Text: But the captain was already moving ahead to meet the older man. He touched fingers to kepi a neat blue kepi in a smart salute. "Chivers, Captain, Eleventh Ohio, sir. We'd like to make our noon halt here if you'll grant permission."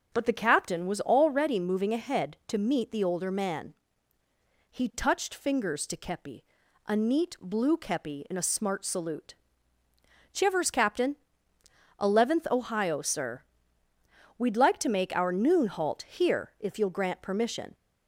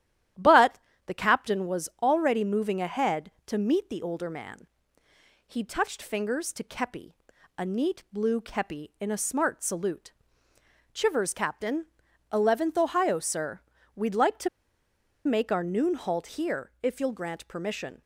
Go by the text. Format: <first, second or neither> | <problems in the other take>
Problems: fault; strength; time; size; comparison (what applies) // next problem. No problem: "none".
first | starts louder than the rest; strong; until 1.6 s; 11.5 dB; also in the first // pauses between "But" and "the"; slight; at 0.7 s; 0.28 s long // pauses between "kepi" and "a"; noticeable; at 7.1 s; 0.46 s long; also in the first // pauses between "to" and "make"; noticeable; at 14.4 s; 0.76 s long